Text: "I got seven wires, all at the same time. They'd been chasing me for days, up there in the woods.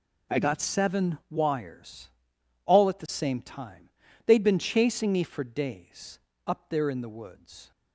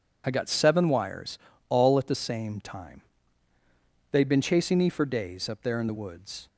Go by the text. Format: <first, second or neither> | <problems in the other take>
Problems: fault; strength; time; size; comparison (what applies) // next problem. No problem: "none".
neither | none